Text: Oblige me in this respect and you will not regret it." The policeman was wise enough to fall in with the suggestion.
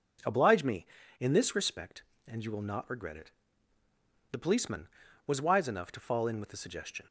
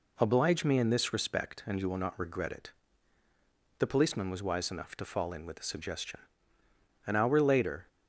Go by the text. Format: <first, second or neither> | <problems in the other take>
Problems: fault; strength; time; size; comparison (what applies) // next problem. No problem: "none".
first | goes on to say "An hour later"; noticeable; from 7.0 s on; 0.82 s long